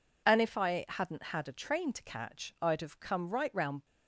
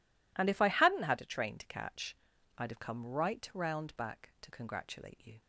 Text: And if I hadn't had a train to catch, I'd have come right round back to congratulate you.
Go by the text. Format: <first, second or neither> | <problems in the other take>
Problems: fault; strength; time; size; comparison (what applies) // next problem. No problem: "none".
second | stops before "back to congratulate you"; at 3.8 s